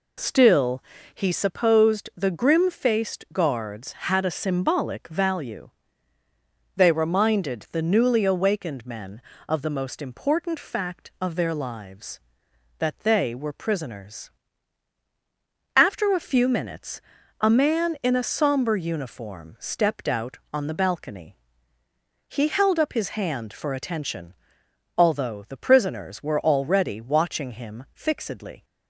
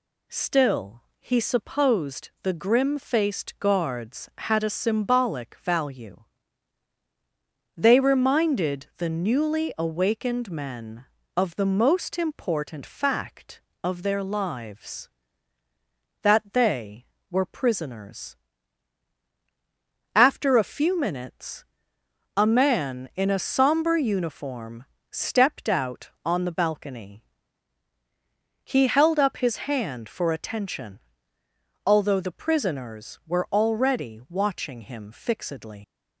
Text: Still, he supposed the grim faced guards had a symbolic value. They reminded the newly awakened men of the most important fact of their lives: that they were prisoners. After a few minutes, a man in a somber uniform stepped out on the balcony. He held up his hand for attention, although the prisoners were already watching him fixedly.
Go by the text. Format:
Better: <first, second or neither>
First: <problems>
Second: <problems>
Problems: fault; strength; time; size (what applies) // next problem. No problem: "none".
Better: first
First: none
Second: pauses between "uniform" and "stepped"; slight; at 24.8 s; 0.26 s long // leaves "fixedly" unfinished; at 35.8 s; 85 ms